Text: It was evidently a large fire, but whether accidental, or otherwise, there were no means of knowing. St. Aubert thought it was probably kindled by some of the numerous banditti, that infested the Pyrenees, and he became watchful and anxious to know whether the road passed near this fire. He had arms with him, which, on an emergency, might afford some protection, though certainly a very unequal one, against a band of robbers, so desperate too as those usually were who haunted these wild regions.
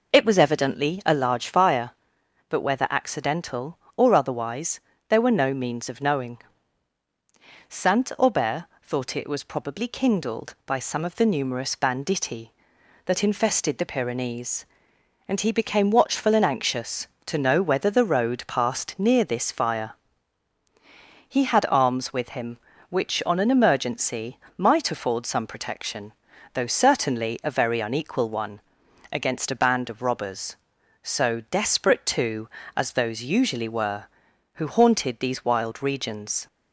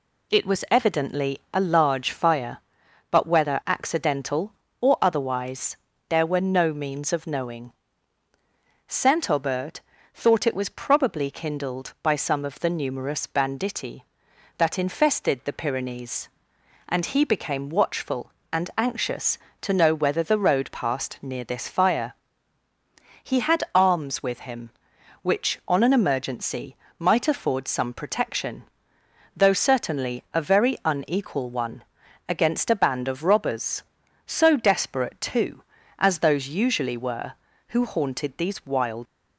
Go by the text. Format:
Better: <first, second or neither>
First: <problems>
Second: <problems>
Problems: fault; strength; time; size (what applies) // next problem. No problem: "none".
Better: first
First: pauses between "Aubert" and "thought"; slight; at 8.6 s; 0.18 s long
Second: pauses between "Aubert" and "thought"; slight; at 9.8 s; 0.32 s long // stops before "regions"; at 39.0 s